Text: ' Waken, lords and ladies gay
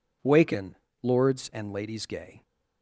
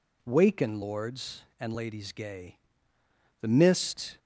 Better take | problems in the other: first | goes on to say "The mist"; noticeable; from 3.4 s on; 0.78 s long

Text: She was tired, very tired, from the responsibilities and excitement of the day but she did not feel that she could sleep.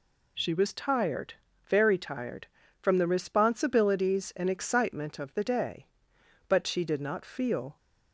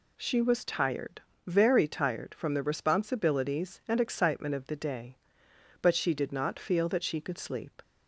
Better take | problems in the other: second | stops before "that she could sleep"; at 7.7 s

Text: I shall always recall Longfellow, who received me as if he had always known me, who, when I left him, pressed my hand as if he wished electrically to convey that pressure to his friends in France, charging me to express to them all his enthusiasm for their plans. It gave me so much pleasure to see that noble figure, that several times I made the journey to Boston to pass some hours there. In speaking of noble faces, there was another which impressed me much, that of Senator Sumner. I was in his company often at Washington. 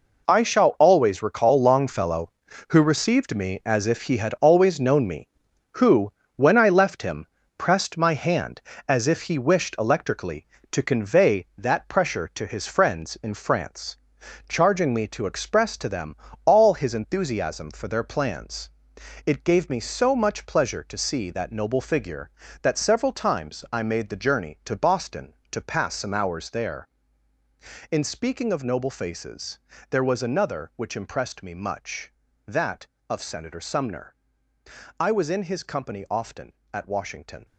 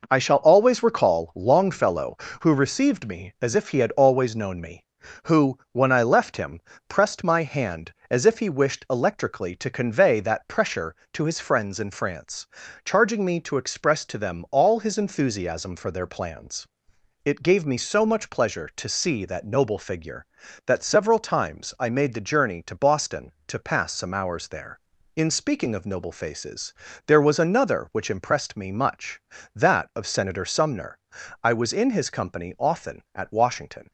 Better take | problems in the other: second | gets quieter; strong; throughout; 10.5 dB // pauses between "them" and "all"; slight; at 16.1 s; 0.30 s long

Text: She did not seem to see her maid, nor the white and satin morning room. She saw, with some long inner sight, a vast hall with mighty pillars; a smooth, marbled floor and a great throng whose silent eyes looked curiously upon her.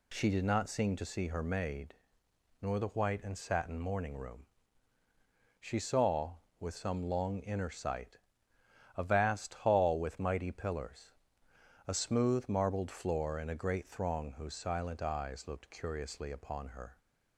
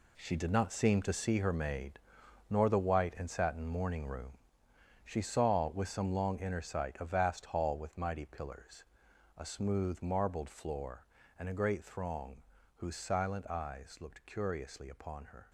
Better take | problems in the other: first | gets quieter; strong; throughout; 10 dB // pauses between "throng" and "whose"; slight; at 12.4 s; 0.34 s long

